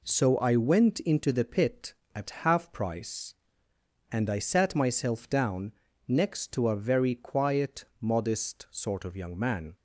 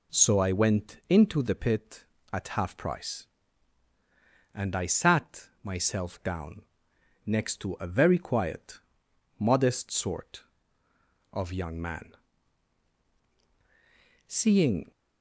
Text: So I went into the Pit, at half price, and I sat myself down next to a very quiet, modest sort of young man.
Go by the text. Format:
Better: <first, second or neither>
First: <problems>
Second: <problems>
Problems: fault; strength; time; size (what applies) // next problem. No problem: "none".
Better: first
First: pauses between "down" and "next"; slight; at 5.7 s; 0.36 s long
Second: pauses between "sat" and "myself"; slight; at 5.4 s; 0.16 s long // pauses between "down" and "next"; noticeable; at 6.6 s; 0.62 s long // goes on to say "Seeing"; noticeable; from 14.2 s on; 0.64 s long